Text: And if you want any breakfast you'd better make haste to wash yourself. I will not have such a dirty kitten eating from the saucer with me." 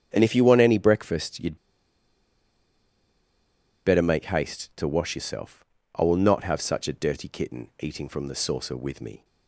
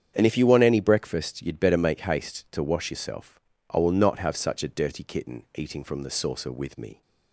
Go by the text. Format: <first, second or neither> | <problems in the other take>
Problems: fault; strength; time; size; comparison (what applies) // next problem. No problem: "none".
second | starts louder than the rest; strong; until 1.1 s; 8 dB; strong in the second // pauses between "you'd" and "better"; strong; at 1.5 s; 2.2 s long